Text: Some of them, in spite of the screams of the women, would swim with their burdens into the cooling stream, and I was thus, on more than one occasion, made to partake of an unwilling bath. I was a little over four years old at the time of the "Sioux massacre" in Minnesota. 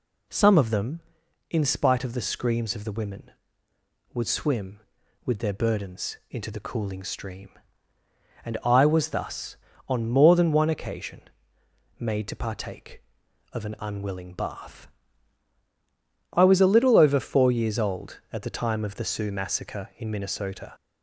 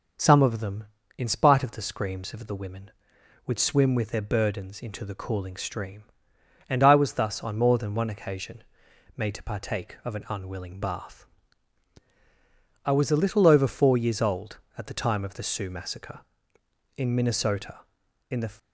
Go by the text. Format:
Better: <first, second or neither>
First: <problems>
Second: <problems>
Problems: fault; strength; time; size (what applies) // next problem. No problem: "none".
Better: first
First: none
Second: goes on to say "In the"; slight; from 18.3 s on; 0.22 s long